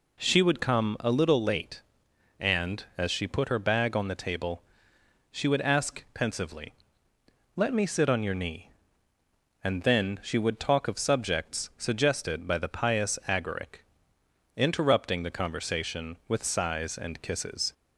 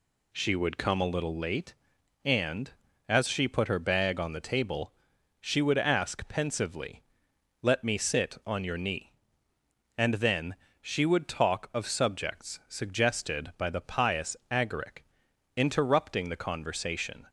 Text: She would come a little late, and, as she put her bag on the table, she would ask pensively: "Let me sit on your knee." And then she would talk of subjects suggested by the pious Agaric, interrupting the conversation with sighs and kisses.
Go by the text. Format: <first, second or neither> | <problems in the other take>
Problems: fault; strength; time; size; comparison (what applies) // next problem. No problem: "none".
first | pauses between "then" and "she"; slight; at 10.5 s; 0.26 s long // stops before "with sighs and kisses"; at 17.2 s